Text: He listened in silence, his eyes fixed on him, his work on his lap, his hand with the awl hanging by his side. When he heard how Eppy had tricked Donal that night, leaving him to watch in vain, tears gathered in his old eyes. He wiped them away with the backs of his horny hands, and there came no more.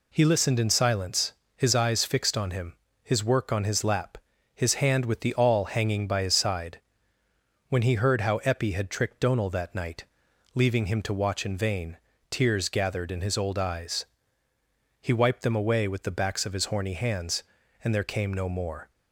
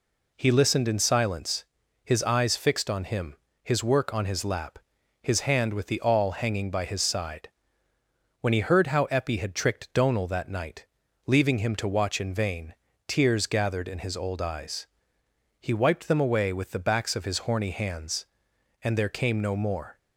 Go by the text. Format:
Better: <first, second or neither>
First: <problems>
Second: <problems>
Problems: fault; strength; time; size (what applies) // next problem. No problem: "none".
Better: neither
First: none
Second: none